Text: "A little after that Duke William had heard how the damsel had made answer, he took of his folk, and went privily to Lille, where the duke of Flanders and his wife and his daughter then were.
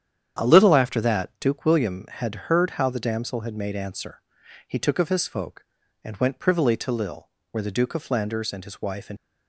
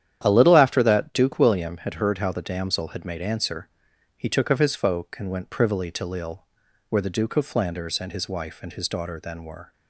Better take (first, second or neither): second